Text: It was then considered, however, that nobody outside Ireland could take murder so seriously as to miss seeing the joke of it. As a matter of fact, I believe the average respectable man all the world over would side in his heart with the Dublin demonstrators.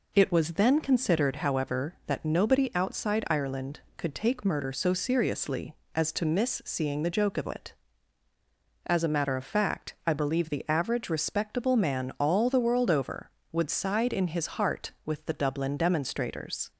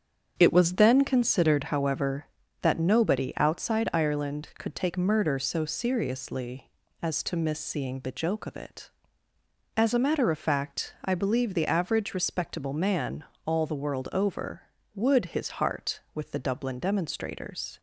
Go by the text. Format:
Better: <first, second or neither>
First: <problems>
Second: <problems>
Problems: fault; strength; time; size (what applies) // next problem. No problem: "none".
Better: first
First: none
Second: starts louder than the rest; strong; until 1.3 s; 7.5 dB // pauses between "man" and "all"; slight; at 13.2 s; 0.22 s long // skips "side in"; at 15.2 s